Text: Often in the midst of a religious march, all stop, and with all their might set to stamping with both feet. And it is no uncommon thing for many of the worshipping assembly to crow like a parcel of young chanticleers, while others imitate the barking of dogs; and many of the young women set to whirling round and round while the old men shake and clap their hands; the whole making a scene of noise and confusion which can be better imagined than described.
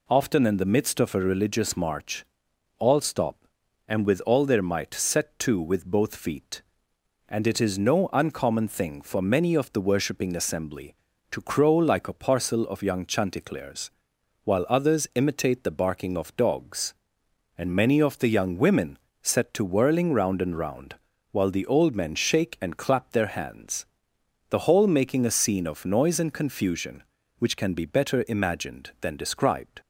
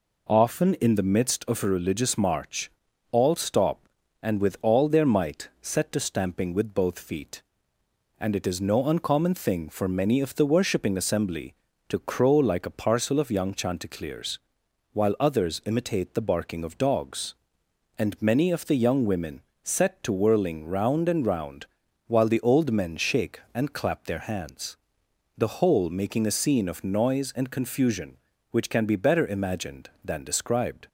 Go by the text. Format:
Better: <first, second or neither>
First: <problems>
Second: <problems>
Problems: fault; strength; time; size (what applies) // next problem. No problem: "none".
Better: second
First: skips "stamping"; at 5.5 s // pauses between "women" and "set"; slight; at 18.9 s; 0.24 s long // pauses between "round" and "while"; slight; at 20.9 s; 0.34 s long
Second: pauses between "women" and "set"; slight; at 19.3 s; 0.24 s long // pauses between "round" and "while"; at 21.6 s; 0.40 s long